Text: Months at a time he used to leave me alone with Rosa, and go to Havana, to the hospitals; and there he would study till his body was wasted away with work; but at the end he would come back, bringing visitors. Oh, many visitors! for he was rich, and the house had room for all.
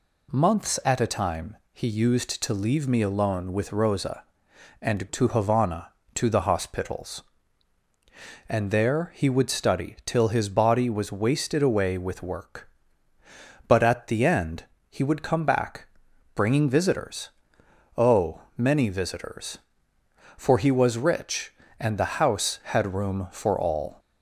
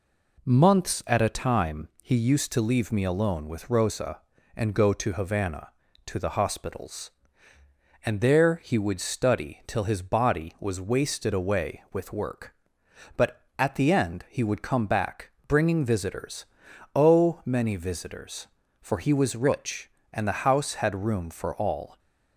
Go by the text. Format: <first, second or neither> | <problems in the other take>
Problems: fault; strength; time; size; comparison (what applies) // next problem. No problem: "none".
second | pauses between "time" and "he"; slight; at 1.5 s; 0.18 s long // skips "go"; at 5.0 s // pauses between "end" and "he"; slight; at 14.6 s; 0.26 s long